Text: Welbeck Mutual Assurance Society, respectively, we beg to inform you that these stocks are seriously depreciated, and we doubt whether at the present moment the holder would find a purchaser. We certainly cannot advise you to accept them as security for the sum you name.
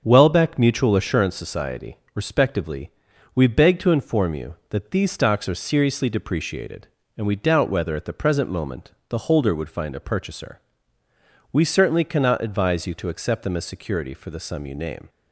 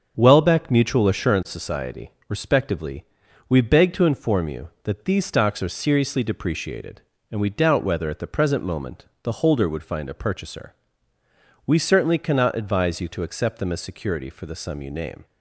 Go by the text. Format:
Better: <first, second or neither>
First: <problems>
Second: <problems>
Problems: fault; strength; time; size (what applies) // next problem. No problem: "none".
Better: neither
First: starts louder than the rest; until 1.0 s; 6.5 dB // pauses between "moment" and "the"; slight; at 8.9 s; 0.18 s long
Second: starts louder than the rest; until 1.1 s; 7 dB // pauses between "moment" and "the"; slight; at 9.0 s; 0.18 s long